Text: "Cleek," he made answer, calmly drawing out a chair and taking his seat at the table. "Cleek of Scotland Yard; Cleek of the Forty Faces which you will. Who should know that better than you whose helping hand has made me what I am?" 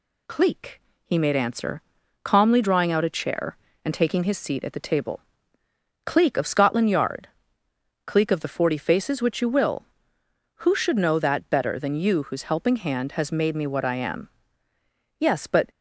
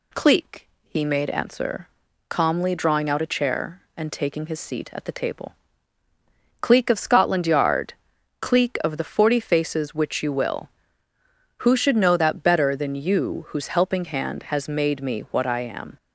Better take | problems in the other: second | goes on to say "Yes but"; from 15.1 s on; 0.52 s long

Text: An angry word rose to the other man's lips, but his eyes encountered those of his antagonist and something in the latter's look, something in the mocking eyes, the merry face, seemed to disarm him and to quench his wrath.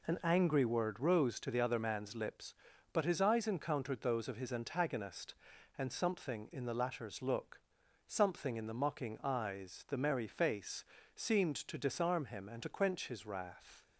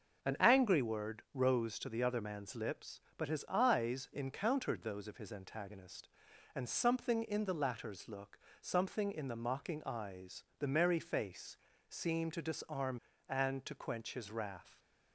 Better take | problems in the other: first | starts louder than the rest; noticeable; until 1.3 s; 6 dB // skips "him"; at 13.1 s

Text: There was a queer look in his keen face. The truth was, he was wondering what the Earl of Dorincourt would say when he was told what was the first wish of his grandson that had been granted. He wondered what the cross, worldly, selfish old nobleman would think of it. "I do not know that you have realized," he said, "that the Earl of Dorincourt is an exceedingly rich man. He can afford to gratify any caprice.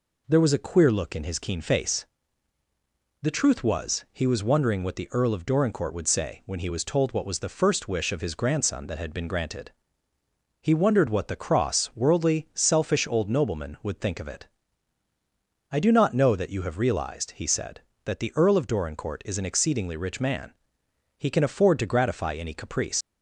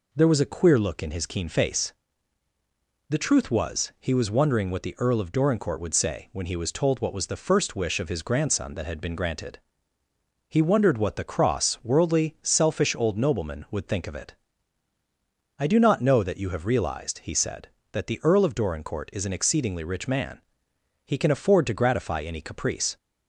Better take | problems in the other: second | leaves "caprice" unfinished; at 23.0 s; 80 ms

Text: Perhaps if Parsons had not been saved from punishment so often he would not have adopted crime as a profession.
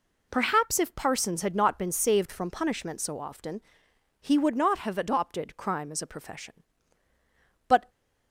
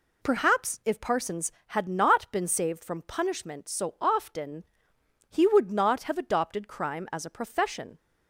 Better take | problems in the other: second | pauses between "often" and "he"; noticeable; at 3.6 s; 0.60 s long; noticeable in the second // goes on to say "But"; slight; from 7.6 s on; 0.22 s long

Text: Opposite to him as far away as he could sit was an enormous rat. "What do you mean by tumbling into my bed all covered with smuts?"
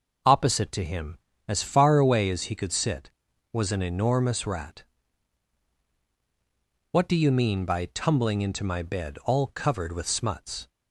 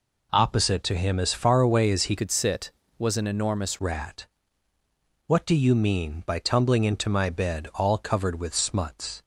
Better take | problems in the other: first | changes voice from "could" to "enormous"; from 2.1 to 3.7 s; 1.6 s long

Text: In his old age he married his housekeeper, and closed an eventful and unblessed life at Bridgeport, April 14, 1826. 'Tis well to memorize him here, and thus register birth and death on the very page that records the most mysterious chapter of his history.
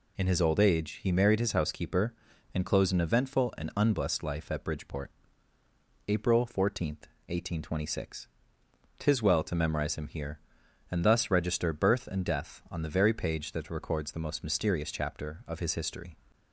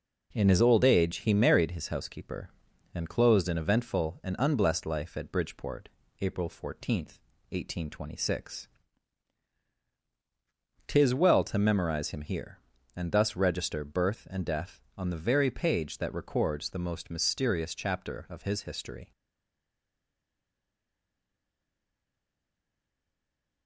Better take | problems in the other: first | stays silent after the last word; strong; from 19.1 s on; 4.5 s long

